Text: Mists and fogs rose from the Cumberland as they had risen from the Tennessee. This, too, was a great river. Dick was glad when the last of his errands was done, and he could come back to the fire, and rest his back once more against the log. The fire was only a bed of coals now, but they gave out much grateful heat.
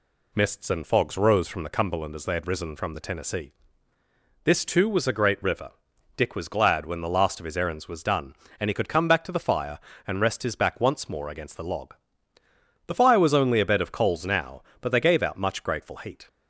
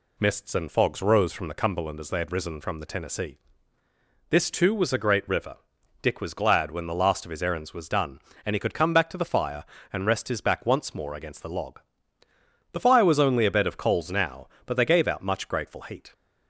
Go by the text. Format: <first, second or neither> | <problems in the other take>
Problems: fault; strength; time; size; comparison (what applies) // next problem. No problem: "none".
neither | none